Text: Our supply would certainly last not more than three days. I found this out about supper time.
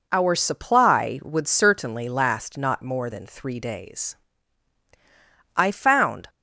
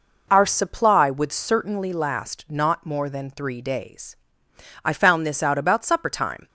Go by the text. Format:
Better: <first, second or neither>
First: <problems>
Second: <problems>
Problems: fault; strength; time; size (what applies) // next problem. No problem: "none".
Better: second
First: stops before "this out about supper time"; at 6.2 s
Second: none